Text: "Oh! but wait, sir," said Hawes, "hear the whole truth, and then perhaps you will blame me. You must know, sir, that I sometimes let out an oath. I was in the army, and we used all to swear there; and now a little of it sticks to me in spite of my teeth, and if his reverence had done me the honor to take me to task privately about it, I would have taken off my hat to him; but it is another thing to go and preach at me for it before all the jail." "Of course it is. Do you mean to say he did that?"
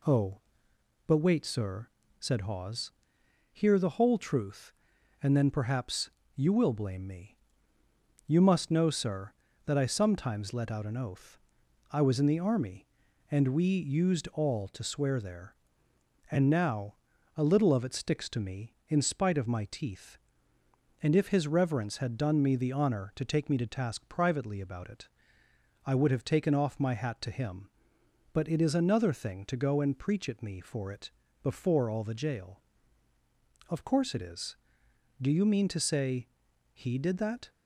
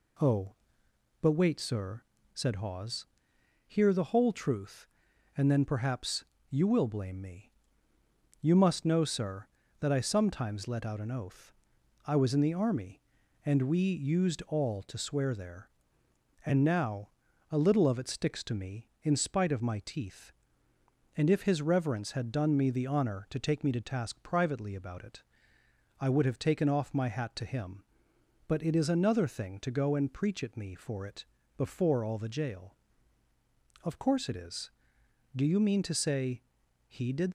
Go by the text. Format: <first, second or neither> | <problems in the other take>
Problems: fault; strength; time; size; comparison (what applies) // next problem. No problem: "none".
first | pauses between "perhaps" and "you"; slight; at 6.2 s; 0.26 s long; slight in the first // pauses between "now" and "a"; at 17.0 s; 0.42 s long; also in the first // pauses between "it" and "before"; slight; at 31.2 s; 0.32 s long; slight in the first // pauses between "say" and "he"; noticeable; at 36.4 s; 0.46 s long; noticeable in the first // stops before "that"; at 37.2 s